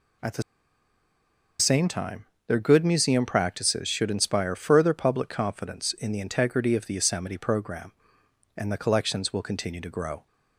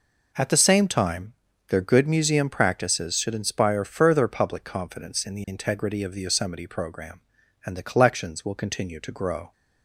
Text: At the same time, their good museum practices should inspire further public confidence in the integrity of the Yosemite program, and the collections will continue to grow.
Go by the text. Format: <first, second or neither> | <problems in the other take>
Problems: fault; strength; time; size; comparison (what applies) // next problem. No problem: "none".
second | pauses between "the" and "same"; at 0.4 s; 1.1 s long